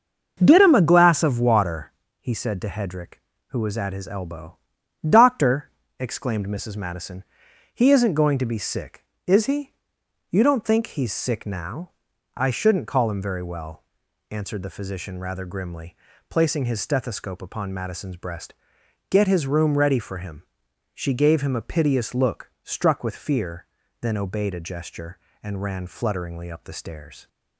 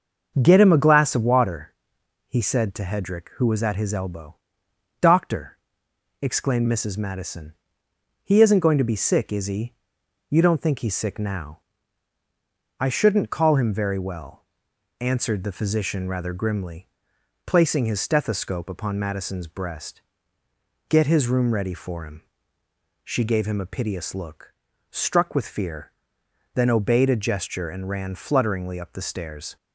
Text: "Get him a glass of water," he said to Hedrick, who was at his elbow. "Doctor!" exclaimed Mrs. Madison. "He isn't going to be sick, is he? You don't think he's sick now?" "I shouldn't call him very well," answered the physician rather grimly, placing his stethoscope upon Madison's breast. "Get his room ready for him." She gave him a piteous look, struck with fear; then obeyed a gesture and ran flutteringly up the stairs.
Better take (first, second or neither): neither